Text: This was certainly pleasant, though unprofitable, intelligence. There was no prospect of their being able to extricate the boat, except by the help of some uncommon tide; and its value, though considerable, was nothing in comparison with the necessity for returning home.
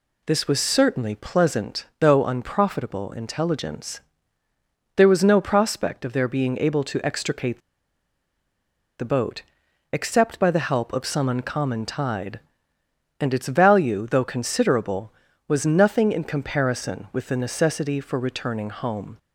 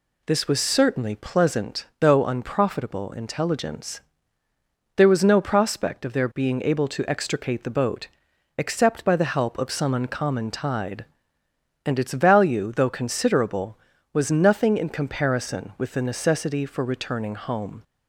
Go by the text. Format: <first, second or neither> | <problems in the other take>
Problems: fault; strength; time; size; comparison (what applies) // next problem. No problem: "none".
second | pauses between "extricate" and "the"; strong; at 7.5 s; 1.4 s long